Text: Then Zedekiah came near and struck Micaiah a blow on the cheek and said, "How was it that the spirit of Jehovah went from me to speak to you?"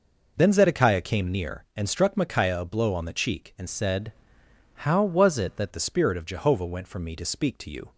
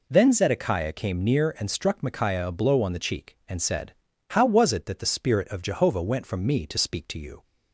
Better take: second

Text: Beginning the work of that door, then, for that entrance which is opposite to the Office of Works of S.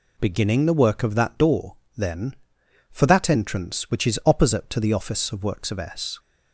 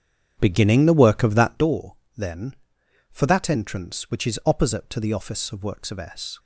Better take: first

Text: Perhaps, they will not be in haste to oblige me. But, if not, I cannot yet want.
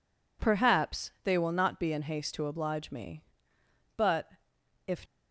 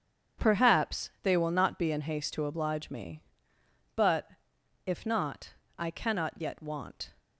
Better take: second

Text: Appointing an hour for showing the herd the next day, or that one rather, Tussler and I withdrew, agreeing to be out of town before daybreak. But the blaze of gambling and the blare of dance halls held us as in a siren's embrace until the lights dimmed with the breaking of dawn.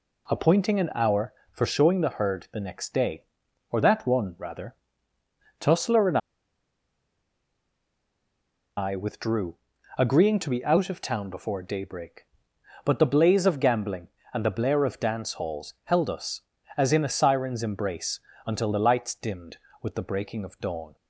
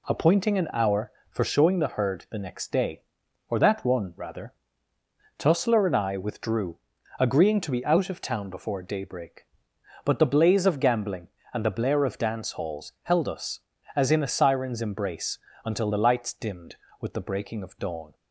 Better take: second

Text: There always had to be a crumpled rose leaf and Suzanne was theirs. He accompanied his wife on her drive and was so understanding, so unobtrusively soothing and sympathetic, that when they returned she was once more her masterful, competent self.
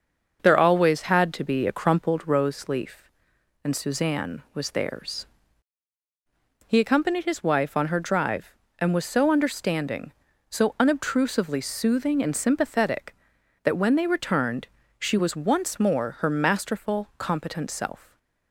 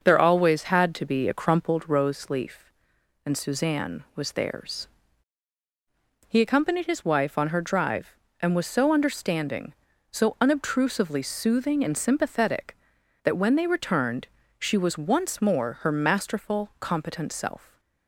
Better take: neither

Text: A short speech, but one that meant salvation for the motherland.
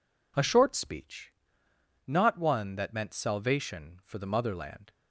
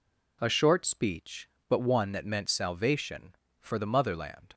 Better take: second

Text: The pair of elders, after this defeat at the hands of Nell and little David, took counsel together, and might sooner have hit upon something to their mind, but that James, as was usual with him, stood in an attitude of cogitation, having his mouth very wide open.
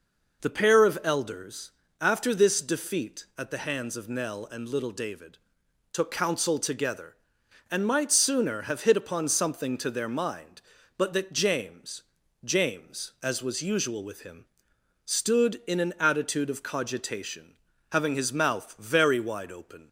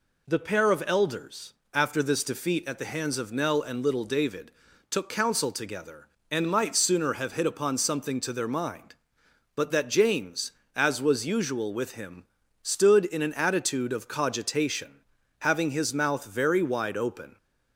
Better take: second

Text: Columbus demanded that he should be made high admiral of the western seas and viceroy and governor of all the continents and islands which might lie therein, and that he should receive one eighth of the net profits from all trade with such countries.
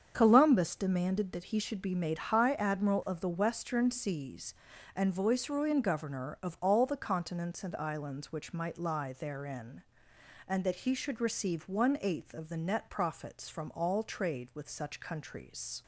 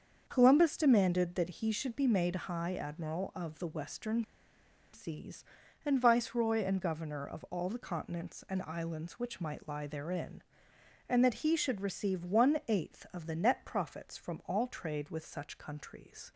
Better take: first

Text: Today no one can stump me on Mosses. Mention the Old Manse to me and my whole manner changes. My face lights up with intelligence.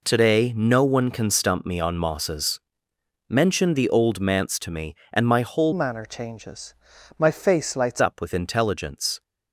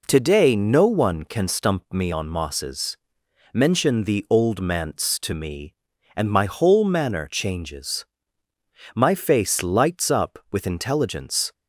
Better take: second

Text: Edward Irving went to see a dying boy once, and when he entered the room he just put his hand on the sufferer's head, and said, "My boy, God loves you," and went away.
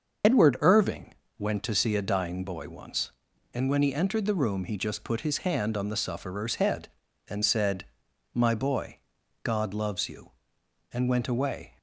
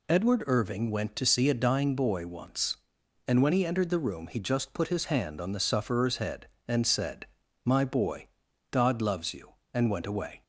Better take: second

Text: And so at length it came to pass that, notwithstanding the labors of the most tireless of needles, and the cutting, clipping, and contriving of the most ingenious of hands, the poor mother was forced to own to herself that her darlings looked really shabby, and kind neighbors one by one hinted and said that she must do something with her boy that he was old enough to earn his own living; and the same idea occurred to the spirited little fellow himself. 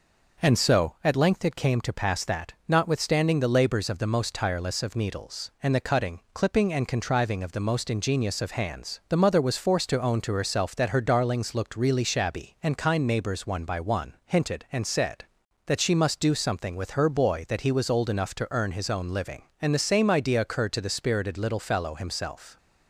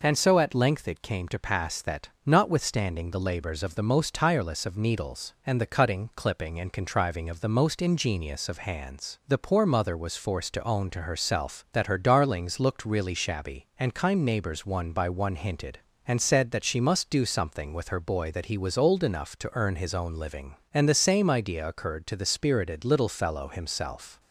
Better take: second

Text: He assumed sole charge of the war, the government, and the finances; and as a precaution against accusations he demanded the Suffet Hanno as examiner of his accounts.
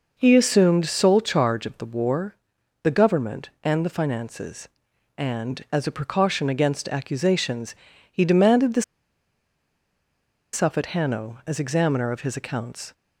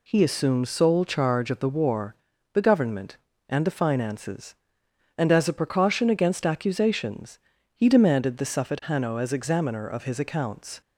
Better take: second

